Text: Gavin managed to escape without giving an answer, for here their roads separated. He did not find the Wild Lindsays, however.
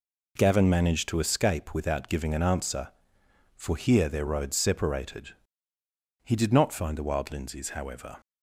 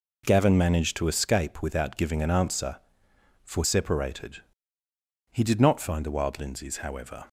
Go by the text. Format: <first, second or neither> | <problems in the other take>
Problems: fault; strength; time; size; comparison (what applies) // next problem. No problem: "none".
first | skips "here their roads"; at 3.6 s